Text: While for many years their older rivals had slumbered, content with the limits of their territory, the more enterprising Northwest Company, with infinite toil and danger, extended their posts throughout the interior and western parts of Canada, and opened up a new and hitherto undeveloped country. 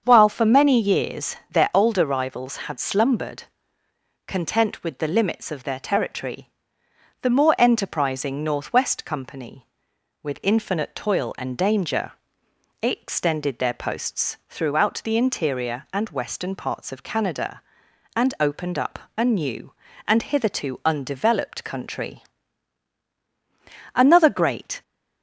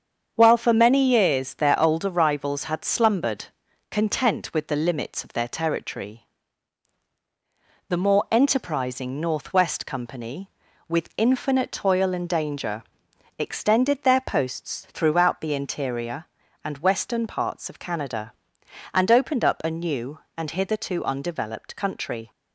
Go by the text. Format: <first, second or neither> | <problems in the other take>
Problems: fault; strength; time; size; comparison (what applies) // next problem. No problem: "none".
second | starts louder than the rest; strong; until 1.0 s; 7 dB; strong in the second // pauses between "up" and "a"; slight; at 18.9 s; 0.18 s long // goes on to say "Another great"; noticeable; from 23.9 s on; 0.88 s long